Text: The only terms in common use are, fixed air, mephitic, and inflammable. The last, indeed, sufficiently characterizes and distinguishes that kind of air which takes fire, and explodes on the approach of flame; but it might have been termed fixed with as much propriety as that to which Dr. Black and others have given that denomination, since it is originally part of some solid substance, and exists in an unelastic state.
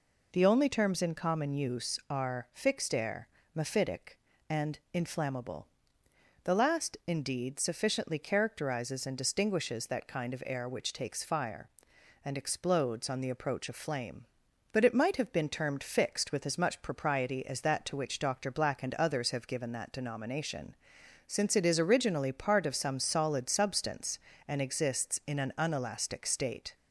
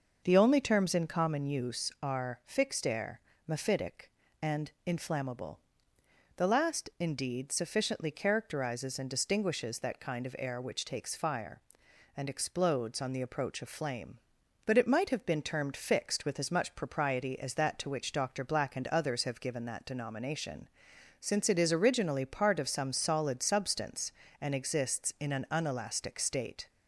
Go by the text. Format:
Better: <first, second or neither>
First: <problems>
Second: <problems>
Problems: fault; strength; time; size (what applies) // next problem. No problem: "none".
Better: first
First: none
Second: starts louder than the rest; noticeable; until 1.4 s; 6 dB